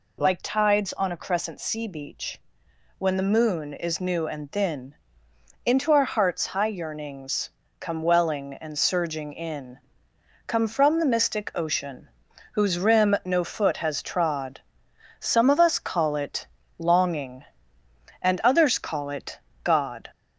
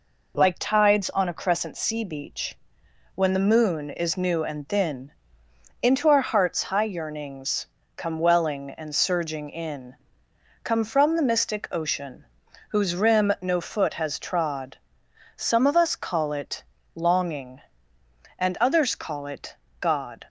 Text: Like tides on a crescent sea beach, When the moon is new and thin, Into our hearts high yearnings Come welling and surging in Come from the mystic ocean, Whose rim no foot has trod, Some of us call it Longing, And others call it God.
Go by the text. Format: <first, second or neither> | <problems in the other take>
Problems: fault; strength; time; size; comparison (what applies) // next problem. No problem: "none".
second | gets louder; slight; throughout; 3 dB // pauses between "yearnings" and "Come"; slight; at 7.4 s; 0.30 s long; slight in the second // pauses between "in" and "Come"; noticeable; at 9.7 s; 0.66 s long; noticeable in the second // pauses between "it" and "Longing"; slight; at 16.4 s; 0.32 s long; slight in the second // pauses between "it" and "God"; slight; at 19.3 s; 0.24 s long; slight in the second